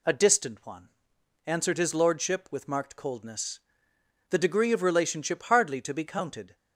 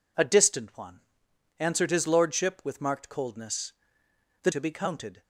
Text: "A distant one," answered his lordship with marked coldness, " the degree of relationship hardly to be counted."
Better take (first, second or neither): first